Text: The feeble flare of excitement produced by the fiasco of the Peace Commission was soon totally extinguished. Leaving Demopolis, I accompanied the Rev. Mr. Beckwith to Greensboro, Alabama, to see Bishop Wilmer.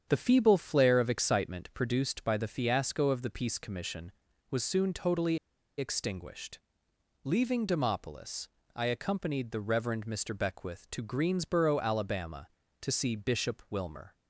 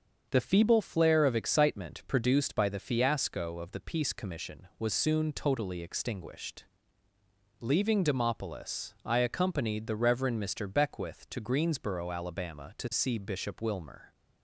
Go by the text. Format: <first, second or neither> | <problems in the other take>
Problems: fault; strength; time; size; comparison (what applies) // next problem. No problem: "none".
second | starts louder than the rest; strong; until 1.1 s; 8 dB; also in the second // pauses between "totally" and "extinguished"; at 5.3 s; 0.40 s long